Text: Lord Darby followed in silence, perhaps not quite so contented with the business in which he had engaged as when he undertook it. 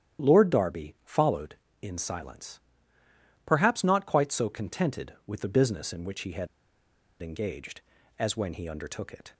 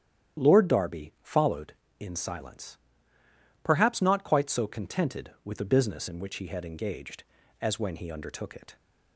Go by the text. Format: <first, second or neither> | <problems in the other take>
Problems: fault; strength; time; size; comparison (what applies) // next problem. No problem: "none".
second | starts louder than the rest; strong; until 1.3 s; 10 dB; strong in the second // pauses between "had" and "engaged"; noticeable; at 6.4 s; 0.75 s long